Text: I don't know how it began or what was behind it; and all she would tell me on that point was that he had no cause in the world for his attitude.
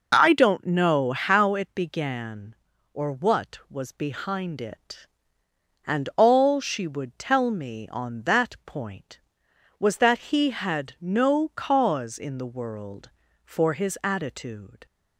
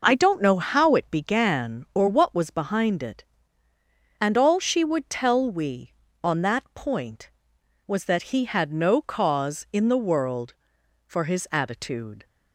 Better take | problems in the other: first | says "we" for "me"; at 5.4 s

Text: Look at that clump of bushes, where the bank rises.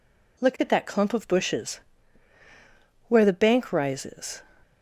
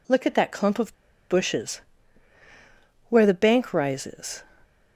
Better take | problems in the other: first | pauses between "of" and "bushes"; at 0.9 s; 0.37 s long

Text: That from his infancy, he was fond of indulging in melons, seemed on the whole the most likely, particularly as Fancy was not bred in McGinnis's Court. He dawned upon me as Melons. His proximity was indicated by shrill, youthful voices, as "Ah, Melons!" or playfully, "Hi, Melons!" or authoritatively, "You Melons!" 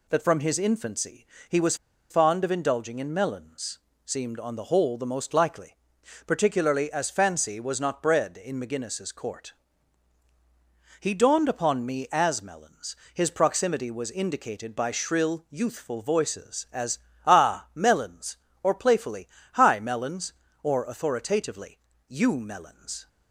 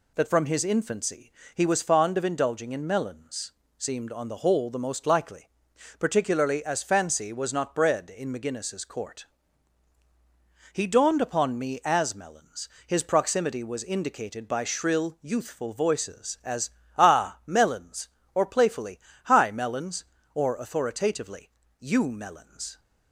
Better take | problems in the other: second | pauses between "was" and "fond"; slight; at 1.7 s; 0.34 s long // pauses between "as" and "Ah"; slight; at 16.9 s; 0.28 s long; slight in the second

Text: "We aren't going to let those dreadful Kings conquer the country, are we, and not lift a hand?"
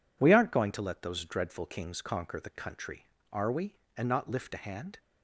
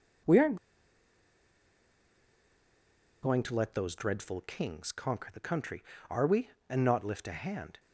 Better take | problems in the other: first | pauses between "aren't" and "going"; strong; at 0.5 s; 2.6 s long

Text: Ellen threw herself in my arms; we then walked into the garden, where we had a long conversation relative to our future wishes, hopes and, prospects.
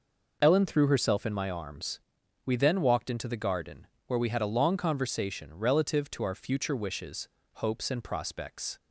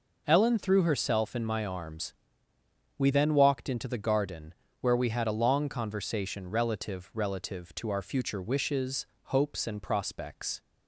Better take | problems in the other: first | says "relative" twice; at 7.1 s

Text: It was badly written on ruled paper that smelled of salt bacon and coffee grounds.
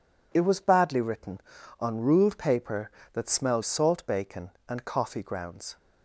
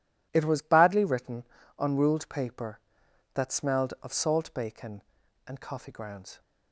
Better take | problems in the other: second | skips "of"; at 3.6 s

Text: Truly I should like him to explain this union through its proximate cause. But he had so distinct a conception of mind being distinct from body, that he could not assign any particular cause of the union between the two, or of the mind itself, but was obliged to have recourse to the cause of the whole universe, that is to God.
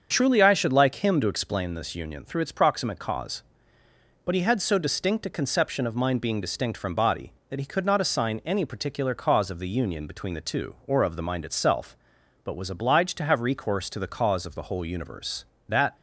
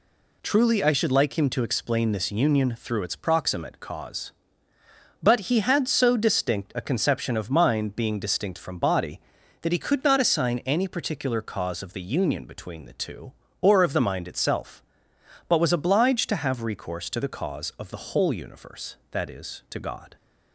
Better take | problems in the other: second | starts louder than the rest; until 1.1 s; 7 dB // stops before "is to God"; at 15.9 s

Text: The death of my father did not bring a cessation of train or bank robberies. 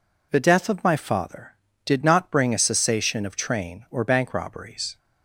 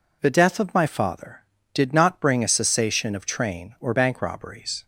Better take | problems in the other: neither | none

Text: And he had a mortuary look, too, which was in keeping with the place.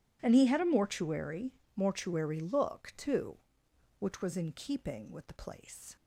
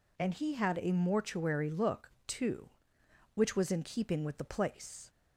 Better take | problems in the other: second | says "mortuary" twice; at 1.7 s

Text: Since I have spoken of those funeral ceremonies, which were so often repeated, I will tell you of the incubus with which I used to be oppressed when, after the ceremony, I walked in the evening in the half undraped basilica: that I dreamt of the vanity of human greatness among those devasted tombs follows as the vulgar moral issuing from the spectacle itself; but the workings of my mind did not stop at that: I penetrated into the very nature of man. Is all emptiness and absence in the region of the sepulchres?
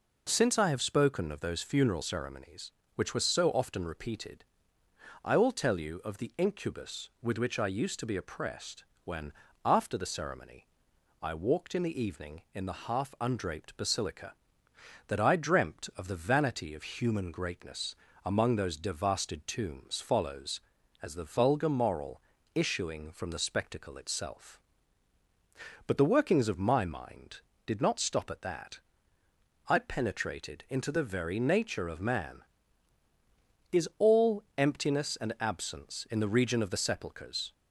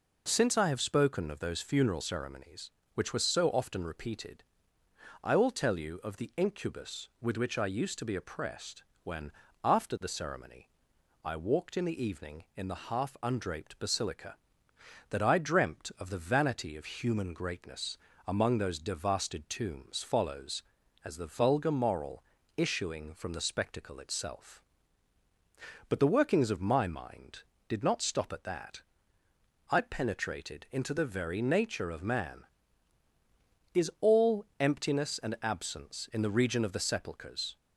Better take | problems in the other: neither | pauses between "oppressed" and "when"; slight; the same in both // pauses between "greatness" and "among"; slight; the same in both // pauses between "moral" and "issuing"; slight; the same in both

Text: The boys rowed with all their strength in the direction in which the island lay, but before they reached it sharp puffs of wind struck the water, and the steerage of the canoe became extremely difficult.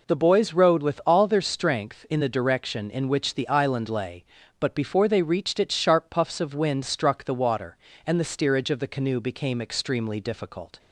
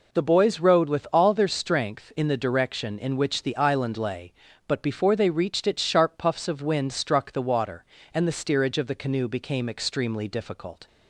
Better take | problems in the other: neither | none

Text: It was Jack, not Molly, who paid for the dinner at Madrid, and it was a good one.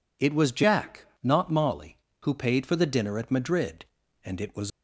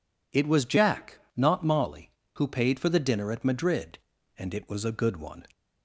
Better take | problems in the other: second | stops before "a good one"; at 4.7 s

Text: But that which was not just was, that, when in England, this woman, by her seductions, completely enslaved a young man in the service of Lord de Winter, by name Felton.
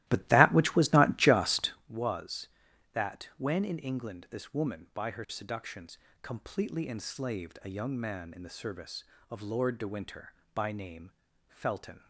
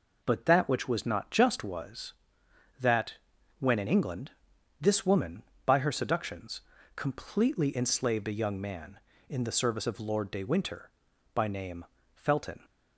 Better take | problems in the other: second | starts louder than the rest; strong; until 1.9 s; 16.5 dB // pauses between "name" and "Felton"; slight; at 11.1 s; 0.36 s long; slight in the second

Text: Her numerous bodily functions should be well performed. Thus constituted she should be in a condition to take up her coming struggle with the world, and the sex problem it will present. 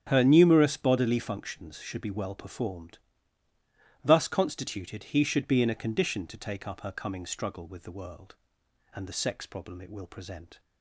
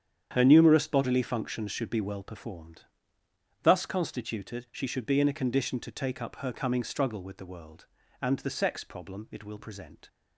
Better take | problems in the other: second | starts louder than the rest; strong; until 1.0 s; 8 dB; strong in the second // says "he" for "she"; at 5.1 s

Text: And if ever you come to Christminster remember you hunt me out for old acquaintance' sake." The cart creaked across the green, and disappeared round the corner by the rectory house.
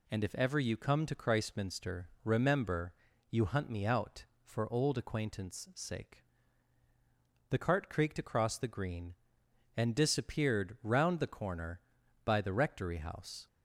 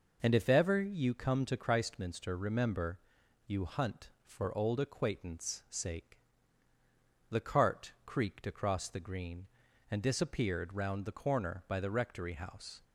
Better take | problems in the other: first | pauses between "remember" and "you"; noticeable; at 2.9 s; 0.48 s long; also in the first // skips "me out"; at 4.1 s

